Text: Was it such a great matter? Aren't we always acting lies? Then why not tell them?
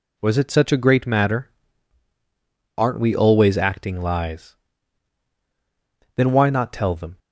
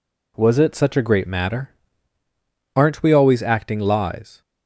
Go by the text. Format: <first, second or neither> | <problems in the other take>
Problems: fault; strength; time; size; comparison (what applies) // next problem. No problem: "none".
first | stops before "Then why not tell them"; at 4.4 s